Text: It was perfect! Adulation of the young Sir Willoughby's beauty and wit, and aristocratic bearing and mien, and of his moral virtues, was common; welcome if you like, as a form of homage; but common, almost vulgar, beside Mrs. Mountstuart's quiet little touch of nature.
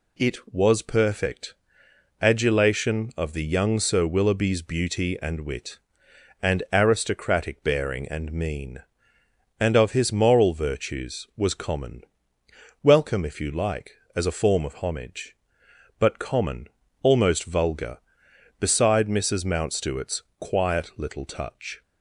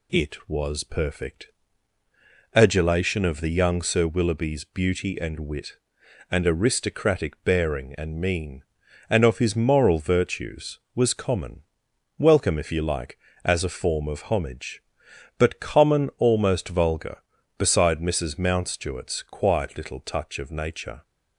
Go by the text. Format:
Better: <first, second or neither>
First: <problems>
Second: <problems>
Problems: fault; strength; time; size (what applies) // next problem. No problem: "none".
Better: second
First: pauses between "Mountstuart's" and "quiet"; slight; at 20.2 s; 0.18 s long // stops before "of nature"; at 21.8 s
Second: none